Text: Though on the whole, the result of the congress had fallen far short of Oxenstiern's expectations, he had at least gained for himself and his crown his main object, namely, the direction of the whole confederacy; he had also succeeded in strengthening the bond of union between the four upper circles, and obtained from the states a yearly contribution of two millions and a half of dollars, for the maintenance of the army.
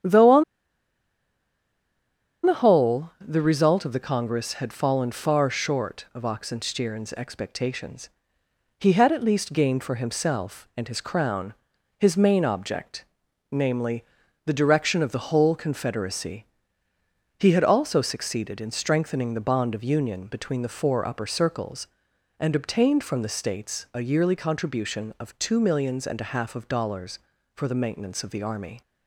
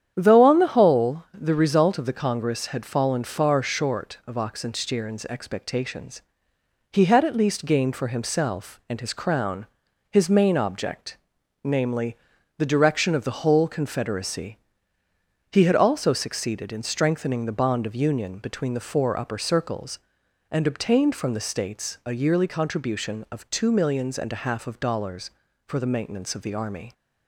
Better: second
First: starts louder than the rest; strong; until 3.0 s; 9 dB // pauses between "on" and "the"; strong; at 0.4 s; 2.0 s long // pauses between "crown" and "his"; noticeable; at 11.5 s; 0.46 s long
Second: starts louder than the rest; strong; until 1.1 s; 9 dB // pauses between "crown" and "his"; noticeable; at 9.6 s; 0.46 s long

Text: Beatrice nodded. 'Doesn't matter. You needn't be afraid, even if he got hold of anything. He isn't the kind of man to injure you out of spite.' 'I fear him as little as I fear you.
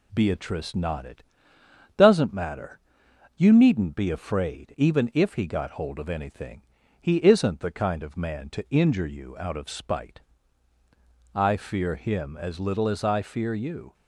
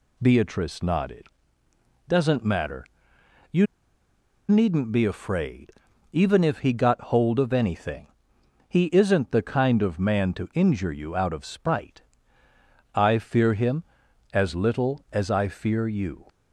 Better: first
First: none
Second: pauses between "You" and "needn't"; noticeable; at 3.6 s; 0.84 s long

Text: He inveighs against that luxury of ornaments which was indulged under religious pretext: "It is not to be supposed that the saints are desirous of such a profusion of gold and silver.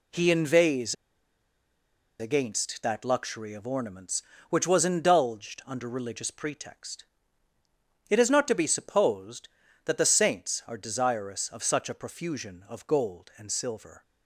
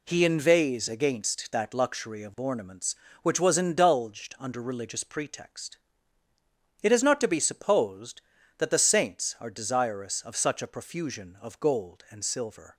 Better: second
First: pauses between "inveighs" and "against"; strong; at 0.9 s; 1.2 s long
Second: none

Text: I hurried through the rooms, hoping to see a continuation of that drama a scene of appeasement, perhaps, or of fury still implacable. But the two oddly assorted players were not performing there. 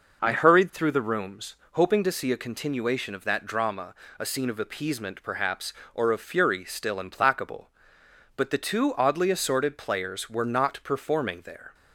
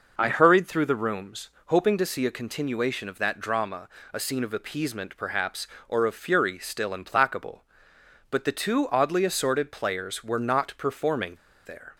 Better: first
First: pauses between "drama" and "a"; slight; at 3.9 s; 0.24 s long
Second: pauses between "drama" and "a"; slight; at 3.8 s; 0.24 s long // pauses between "performing" and "there"; slight; at 11.3 s; 0.29 s long

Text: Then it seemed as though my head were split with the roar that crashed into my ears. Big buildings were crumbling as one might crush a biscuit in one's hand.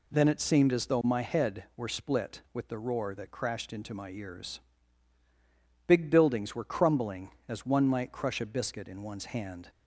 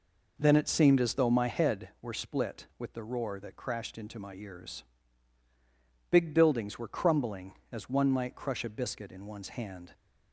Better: first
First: none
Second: starts louder than the rest; noticeable; until 1.8 s; 4.5 dB

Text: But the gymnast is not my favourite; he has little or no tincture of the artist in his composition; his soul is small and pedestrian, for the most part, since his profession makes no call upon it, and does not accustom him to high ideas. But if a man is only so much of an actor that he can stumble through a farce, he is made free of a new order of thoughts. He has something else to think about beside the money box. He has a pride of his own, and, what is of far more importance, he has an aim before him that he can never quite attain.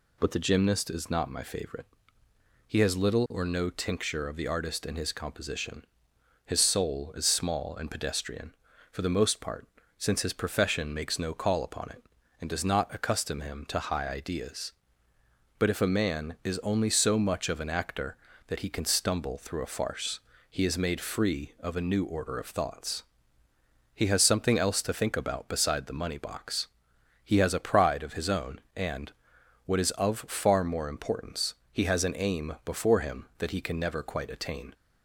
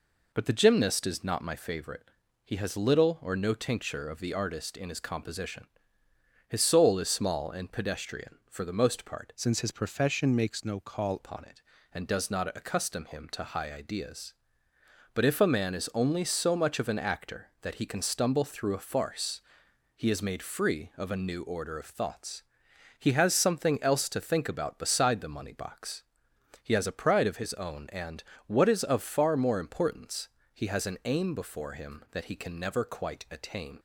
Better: first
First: none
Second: changes voice from "since" to "call"; from 9.3 to 11.1 s; 1.8 s long

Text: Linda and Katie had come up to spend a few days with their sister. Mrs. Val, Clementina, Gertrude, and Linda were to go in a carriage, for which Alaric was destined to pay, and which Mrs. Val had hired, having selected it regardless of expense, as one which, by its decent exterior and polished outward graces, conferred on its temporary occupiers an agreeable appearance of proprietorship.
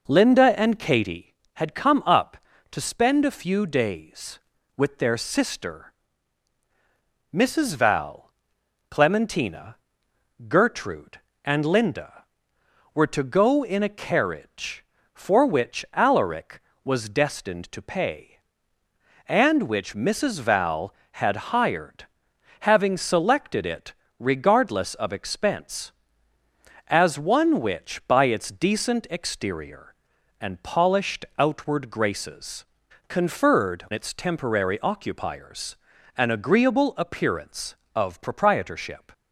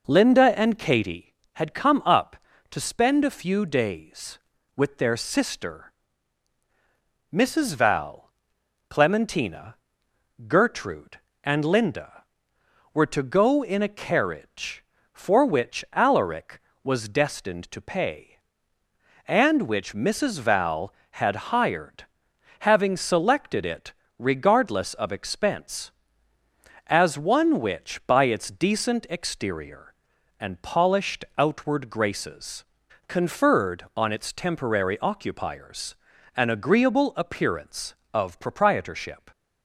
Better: second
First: pauses between "it" and "regardless"; slight; at 23.9 s; 0.28 s long // skips "on"; at 33.8 s // pauses between "occupiers" and "an"; at 35.7 s; 0.40 s long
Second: pauses between "it" and "regardless"; slight; at 23.9 s; 0.28 s long // pauses between "occupiers" and "an"; at 35.9 s; 0.40 s long

